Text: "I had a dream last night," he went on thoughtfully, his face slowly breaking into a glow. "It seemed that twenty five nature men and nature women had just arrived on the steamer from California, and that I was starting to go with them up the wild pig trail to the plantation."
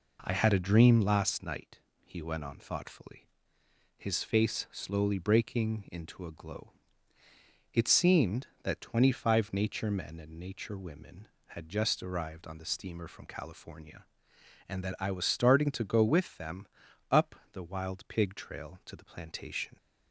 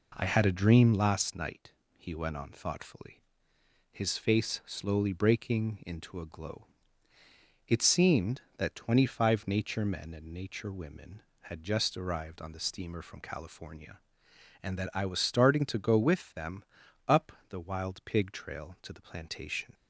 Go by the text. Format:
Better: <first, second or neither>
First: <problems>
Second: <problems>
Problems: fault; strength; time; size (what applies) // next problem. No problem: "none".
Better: neither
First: pauses between "them" and "up"; at 16.6 s; 0.42 s long // pauses between "up" and "the"; slight; at 17.3 s; 0.16 s long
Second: pauses between "them" and "up"; at 16.6 s; 0.42 s long // pauses between "up" and "the"; slight; at 17.3 s; 0.16 s long